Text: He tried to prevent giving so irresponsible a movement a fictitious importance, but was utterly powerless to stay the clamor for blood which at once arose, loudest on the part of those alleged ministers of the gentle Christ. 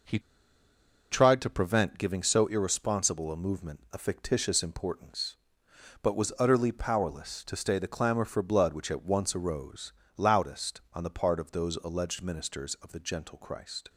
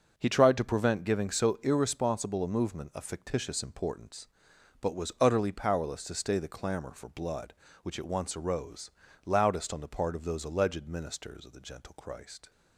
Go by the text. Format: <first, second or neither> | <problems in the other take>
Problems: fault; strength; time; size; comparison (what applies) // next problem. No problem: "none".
second | pauses between "He" and "tried"; noticeable; at 0.1 s; 0.92 s long